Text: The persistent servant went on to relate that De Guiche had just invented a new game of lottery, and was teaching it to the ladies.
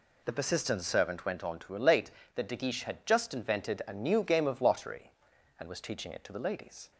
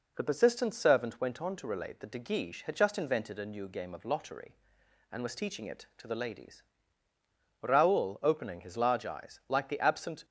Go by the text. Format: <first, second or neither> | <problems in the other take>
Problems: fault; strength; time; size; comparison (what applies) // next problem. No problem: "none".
first | goes on to say "Raoul opening his large eyes like the absent"; strong; from 7.6 s on; 2.6 s long